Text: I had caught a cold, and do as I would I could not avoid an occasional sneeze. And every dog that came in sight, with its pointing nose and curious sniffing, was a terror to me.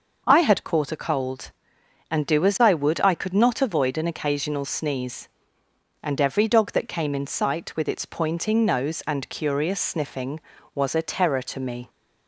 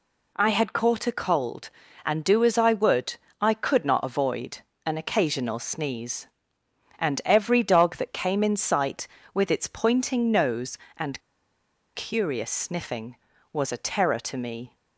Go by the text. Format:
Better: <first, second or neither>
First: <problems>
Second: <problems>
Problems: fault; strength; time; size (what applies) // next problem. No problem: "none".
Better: first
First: none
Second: pauses between "would" and "I"; slight; at 3.1 s; 0.26 s long // pauses between "avoid" and "an"; slight; at 4.5 s; 0.26 s long // pauses between "and" and "curious"; noticeable; at 11.2 s; 0.74 s long